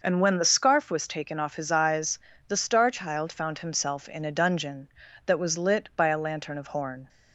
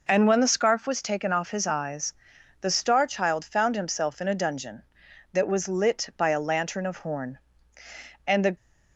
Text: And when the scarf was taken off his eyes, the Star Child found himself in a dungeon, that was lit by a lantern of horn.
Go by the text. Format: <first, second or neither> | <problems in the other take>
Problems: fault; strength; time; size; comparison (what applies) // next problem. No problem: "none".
first | goes on to say "And the"; slight; from 8.2 s on; 0.30 s long